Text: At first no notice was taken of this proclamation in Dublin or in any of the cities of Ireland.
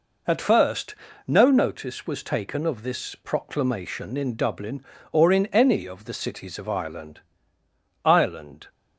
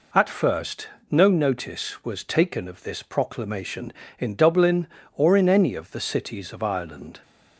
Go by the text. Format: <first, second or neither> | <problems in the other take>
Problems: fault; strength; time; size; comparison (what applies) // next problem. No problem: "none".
second | pauses between "first" and "no"; slight; at 0.9 s; 0.32 s long; slight in the second // says "Ireland" twice; at 8.0 s